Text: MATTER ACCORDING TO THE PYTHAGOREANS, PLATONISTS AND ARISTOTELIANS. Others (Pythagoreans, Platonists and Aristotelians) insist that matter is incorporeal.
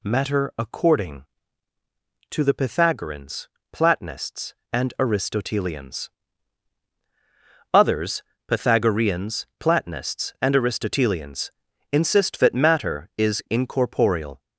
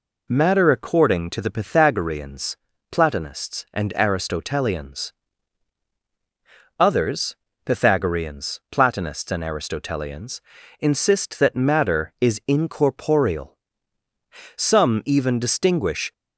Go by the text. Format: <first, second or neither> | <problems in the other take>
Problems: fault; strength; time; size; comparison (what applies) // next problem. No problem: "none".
first | goes on to say "Some even distinguish"; from 14.5 s on; 1.5 s long